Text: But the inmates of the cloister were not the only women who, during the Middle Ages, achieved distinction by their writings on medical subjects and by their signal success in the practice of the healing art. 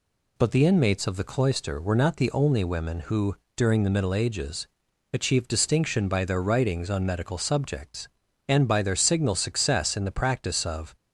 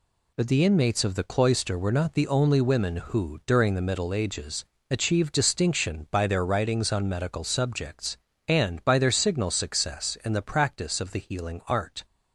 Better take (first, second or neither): second